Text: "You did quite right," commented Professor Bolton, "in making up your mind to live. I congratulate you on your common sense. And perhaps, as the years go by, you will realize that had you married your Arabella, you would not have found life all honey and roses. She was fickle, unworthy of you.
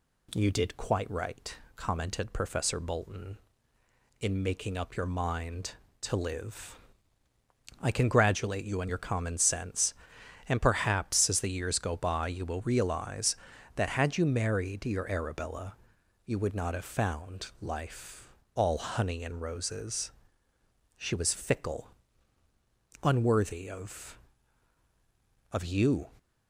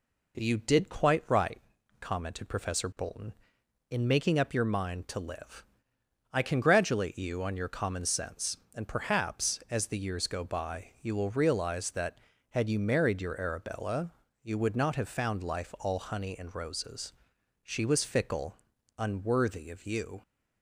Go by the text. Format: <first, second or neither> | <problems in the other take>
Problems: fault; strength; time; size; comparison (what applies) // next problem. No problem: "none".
second | pauses between "life" and "all"; slight; at 18.2 s; 0.24 s long // says "of" twice; at 25.5 s